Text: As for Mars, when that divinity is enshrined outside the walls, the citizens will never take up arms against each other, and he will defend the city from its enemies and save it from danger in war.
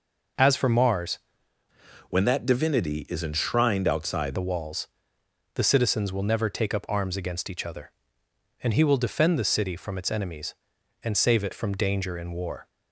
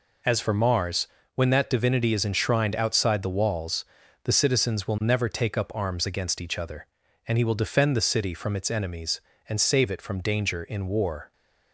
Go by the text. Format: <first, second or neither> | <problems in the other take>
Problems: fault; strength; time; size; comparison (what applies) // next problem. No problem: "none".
second | changes voice from "when" to "outside"; from 2.0 to 4.3 s; 2.3 s long